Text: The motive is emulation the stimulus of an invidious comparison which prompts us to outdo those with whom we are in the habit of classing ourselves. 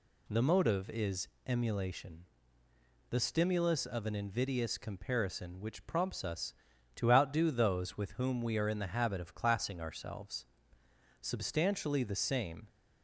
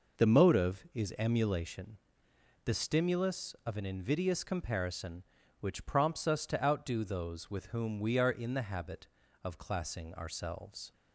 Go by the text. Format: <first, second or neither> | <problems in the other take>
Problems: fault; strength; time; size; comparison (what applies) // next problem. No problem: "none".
second | pauses between "is" and "emulation"; slight; at 1.2 s; 0.18 s long // pauses between "emulation" and "the"; noticeable; at 2.2 s; 0.86 s long; noticeable in the second // goes on to say "Substantially the same"; from 11.2 s on; 1.4 s long